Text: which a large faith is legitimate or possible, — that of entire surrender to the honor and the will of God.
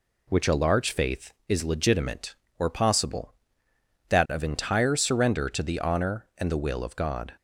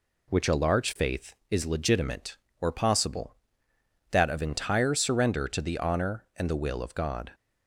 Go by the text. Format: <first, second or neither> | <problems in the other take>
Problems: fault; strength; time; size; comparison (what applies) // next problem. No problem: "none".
neither | none